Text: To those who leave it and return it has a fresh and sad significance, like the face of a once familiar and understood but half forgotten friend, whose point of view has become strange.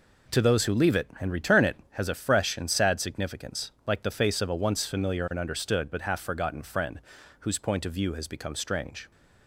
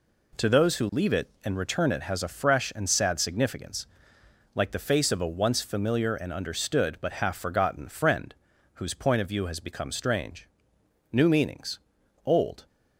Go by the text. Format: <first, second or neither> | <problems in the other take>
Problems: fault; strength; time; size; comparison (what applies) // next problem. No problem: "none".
first | goes on to say "New meanings old"; from 11.1 s on; 1.5 s long